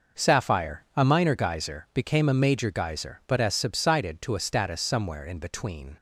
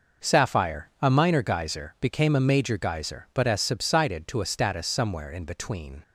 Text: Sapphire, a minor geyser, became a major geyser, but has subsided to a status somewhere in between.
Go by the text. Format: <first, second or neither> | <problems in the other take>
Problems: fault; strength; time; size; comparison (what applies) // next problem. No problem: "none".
neither | none